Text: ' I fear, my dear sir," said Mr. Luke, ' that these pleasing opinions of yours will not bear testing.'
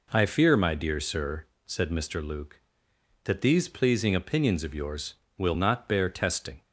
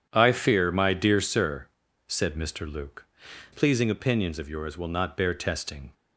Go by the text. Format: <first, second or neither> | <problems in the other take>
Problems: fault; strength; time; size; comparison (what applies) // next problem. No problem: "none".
first | starts louder than the rest; strong; until 1.1 s; 8.5 dB // skips "that these"; at 3.5 s